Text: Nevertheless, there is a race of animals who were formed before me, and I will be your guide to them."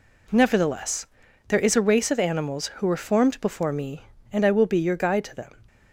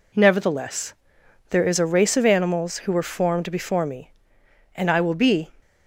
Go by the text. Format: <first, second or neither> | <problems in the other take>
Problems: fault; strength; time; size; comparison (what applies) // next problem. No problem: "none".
first | stops before "your guide to them"; at 5.6 s